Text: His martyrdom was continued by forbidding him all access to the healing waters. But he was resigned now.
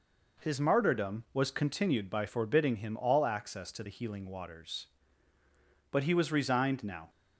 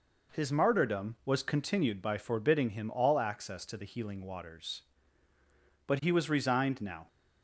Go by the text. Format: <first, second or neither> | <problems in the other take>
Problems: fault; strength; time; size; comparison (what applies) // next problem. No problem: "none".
neither | none